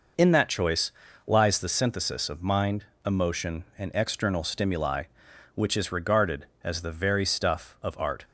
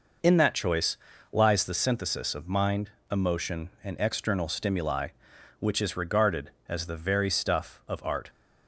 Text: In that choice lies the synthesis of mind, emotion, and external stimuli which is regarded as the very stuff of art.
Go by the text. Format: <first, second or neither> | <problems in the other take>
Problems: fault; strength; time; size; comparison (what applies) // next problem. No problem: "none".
neither | pauses between "choice" and "lies"; slight; the same in both